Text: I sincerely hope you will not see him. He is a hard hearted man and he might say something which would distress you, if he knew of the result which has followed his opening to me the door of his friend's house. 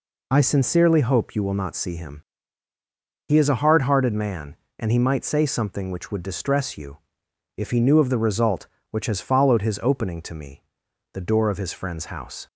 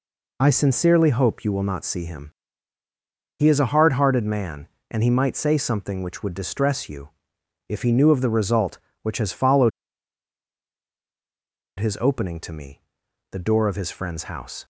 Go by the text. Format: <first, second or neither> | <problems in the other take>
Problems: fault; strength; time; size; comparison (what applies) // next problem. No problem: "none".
first | pauses between "followed" and "his"; strong; at 9.7 s; 2.0 s long // pauses between "me" and "the"; noticeable; at 12.8 s; 0.50 s long; noticeable in the first